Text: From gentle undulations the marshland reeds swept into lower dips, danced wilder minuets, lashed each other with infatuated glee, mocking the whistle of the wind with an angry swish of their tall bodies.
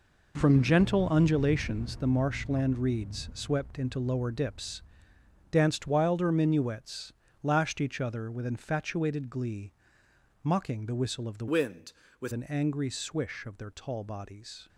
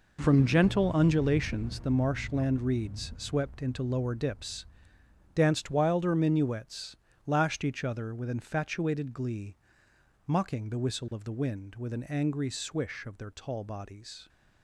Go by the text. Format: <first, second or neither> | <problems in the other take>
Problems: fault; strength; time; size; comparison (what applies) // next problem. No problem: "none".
second | changes voice from "wind" to "with"; from 11.4 to 12.3 s; 0.9 s long